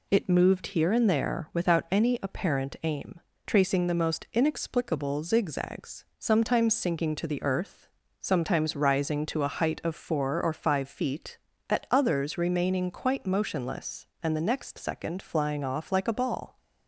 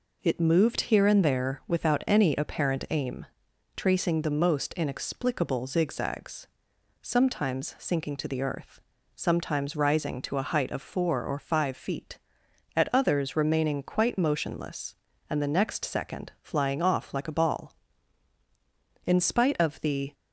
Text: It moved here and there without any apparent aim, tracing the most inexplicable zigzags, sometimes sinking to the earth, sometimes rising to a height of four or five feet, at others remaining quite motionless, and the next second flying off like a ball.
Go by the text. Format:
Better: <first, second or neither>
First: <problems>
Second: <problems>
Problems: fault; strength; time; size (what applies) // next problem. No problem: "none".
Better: first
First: none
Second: goes on to say "In spite of the"; noticeable; from 19.0 s on; 1.0 s long